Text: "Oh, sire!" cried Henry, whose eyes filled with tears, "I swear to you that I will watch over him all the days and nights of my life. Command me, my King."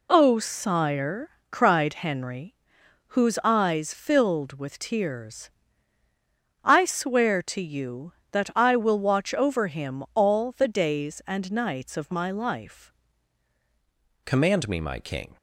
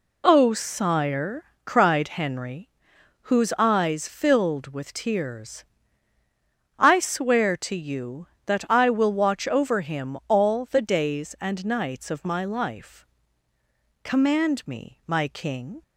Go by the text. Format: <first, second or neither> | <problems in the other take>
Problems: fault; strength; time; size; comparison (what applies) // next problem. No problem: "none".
second | changes voice at "Command"; from 14.2 s on; 1.1 s long